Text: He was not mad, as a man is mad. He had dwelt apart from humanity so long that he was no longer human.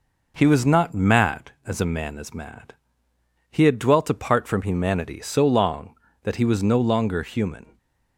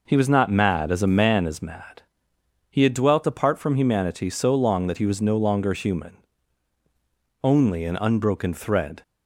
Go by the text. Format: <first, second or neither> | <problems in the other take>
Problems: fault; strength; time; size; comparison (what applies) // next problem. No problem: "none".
first | goes on to say "Only an unbroken thread"; from 7.4 s on; 1.6 s long